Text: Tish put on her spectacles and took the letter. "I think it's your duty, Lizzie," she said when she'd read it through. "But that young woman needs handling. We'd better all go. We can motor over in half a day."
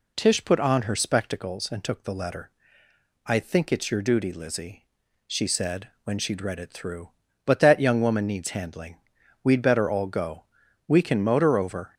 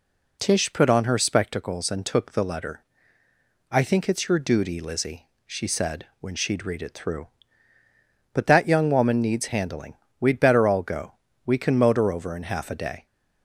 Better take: second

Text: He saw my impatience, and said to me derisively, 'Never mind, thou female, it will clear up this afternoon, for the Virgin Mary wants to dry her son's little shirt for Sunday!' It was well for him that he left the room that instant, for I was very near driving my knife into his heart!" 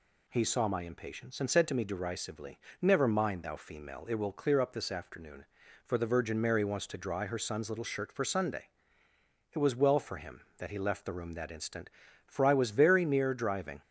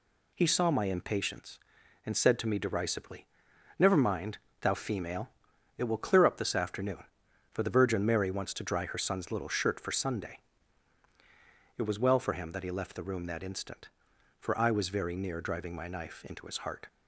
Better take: second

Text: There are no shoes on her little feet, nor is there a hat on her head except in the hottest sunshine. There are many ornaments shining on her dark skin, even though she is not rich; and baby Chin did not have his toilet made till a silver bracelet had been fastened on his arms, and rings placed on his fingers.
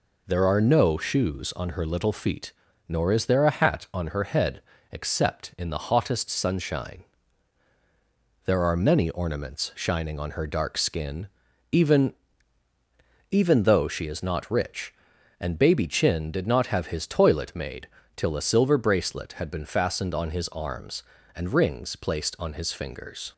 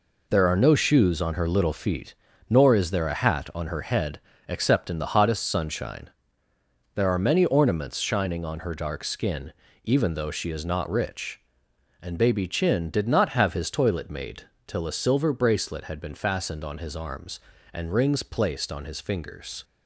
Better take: second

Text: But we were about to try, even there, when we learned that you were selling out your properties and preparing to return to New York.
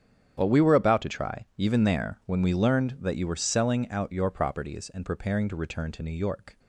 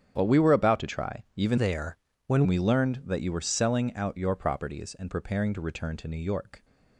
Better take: first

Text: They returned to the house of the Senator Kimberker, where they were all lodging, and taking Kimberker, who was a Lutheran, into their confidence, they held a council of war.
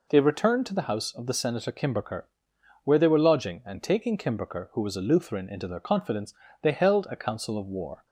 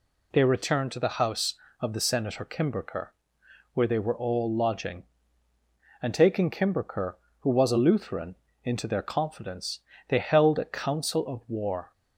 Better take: second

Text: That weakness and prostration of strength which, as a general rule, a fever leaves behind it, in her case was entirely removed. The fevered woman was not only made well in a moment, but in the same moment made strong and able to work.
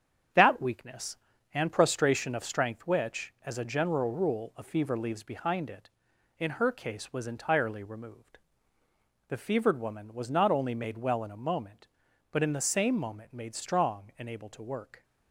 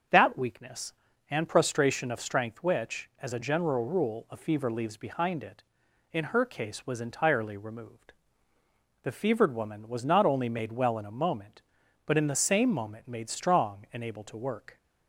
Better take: second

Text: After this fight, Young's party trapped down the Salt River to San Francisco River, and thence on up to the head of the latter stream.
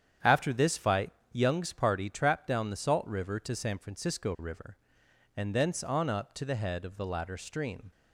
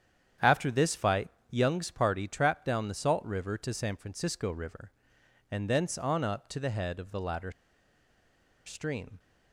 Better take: first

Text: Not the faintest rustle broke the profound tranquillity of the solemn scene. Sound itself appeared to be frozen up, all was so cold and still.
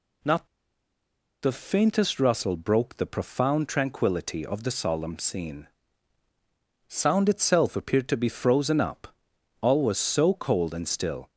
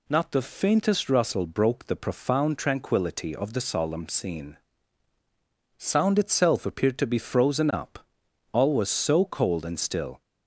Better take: second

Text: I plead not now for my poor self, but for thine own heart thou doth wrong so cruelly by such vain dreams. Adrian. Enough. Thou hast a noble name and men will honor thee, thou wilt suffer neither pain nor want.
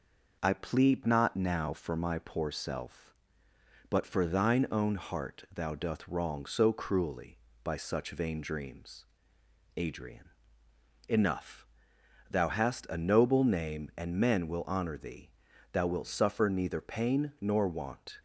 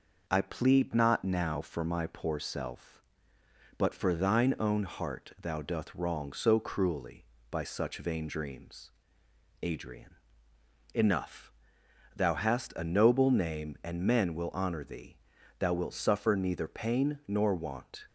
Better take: neither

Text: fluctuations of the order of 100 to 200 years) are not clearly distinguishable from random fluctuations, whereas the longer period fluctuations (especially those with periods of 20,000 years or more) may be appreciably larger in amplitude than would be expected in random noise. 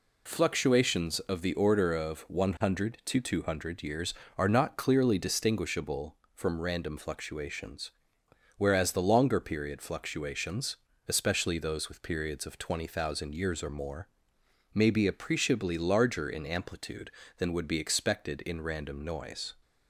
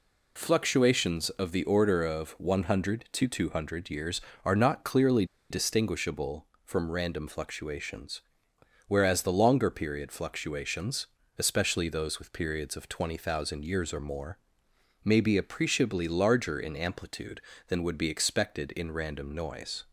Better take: first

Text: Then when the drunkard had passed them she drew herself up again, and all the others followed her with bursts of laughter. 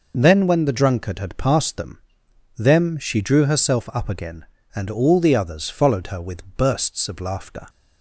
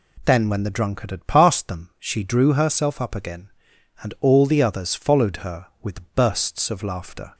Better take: second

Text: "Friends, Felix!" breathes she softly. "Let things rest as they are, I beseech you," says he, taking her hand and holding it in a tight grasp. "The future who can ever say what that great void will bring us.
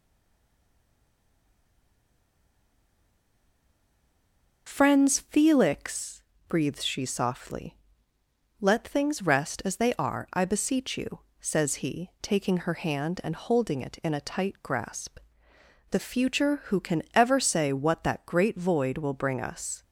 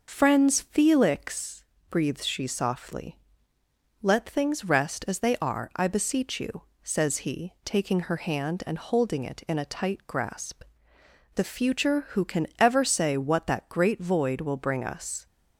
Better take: second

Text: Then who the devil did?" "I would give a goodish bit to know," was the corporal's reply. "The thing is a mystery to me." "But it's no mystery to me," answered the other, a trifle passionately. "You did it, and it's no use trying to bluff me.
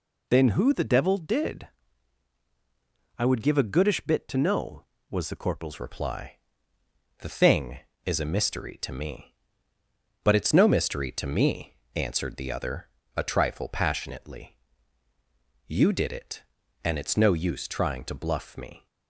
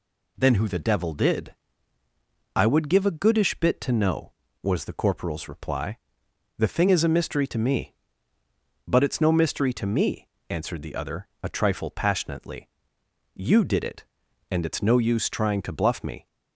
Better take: second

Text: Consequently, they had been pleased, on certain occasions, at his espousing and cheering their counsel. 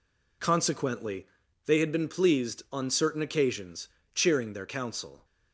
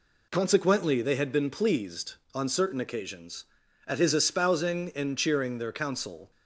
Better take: second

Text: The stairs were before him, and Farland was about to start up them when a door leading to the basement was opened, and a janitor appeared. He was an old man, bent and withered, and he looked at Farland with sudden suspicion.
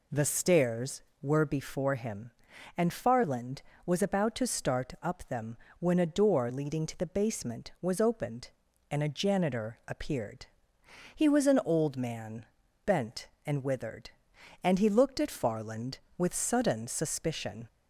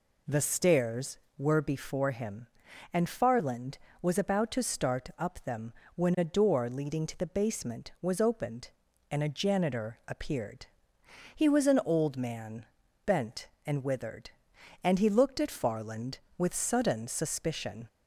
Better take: neither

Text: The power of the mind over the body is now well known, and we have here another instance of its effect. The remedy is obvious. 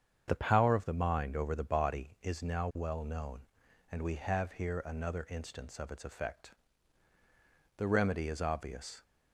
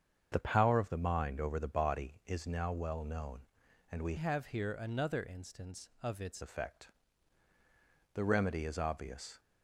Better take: first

